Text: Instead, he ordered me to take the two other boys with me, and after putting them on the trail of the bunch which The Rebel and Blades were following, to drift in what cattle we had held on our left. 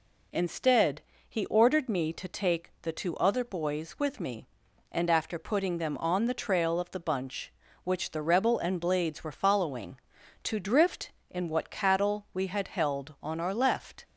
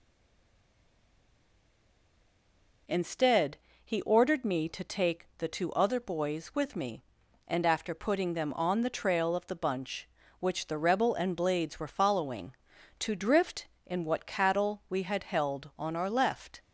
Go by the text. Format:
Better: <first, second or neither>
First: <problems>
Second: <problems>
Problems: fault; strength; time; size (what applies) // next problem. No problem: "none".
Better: first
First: none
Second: stays silent before the first word; strong; until 2.8 s; 2.8 s long